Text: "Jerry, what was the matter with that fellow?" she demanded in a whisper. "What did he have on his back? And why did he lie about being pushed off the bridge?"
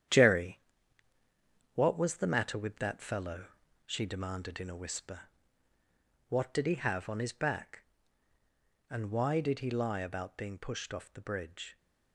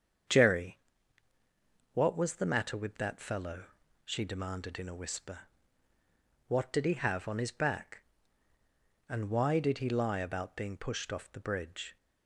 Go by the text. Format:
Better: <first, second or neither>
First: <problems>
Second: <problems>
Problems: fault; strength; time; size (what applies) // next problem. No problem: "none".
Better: second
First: gets quieter; strong; throughout; 8.5 dB // starts louder than the rest; strong; until 2.2 s; 9.5 dB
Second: starts louder than the rest; strong; until 2.4 s; 7.5 dB